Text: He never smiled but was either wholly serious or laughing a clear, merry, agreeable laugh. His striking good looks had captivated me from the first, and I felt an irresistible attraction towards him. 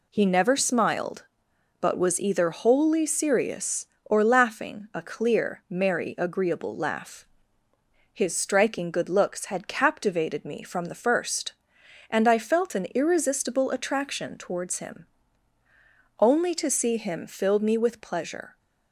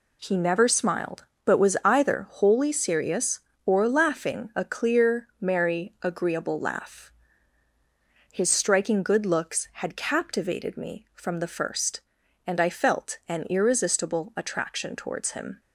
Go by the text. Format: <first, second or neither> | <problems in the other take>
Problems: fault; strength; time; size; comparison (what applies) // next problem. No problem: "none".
second | goes on to say "Only to see him filled me with pleasure"; strong; from 16.1 s on; 2.4 s long